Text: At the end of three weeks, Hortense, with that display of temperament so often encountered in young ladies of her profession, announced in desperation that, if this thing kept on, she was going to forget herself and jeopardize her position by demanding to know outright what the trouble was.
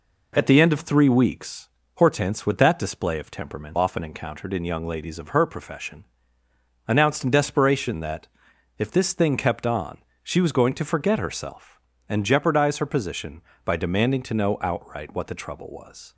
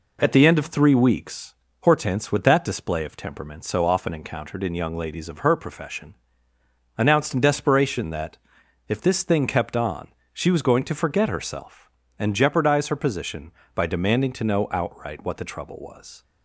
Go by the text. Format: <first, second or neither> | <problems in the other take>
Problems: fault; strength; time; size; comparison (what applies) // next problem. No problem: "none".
second | skips "so"; at 3.7 s